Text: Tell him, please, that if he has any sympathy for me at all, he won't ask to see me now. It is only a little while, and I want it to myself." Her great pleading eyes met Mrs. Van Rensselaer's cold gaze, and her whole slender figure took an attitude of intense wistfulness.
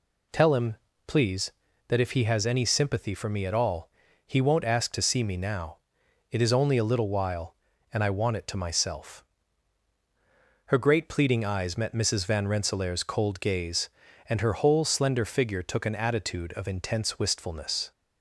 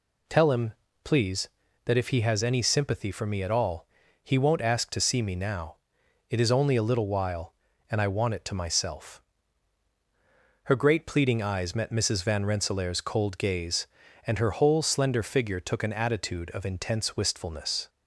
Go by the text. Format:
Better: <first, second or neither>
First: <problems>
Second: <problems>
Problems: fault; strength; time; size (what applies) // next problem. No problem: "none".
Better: neither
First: none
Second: none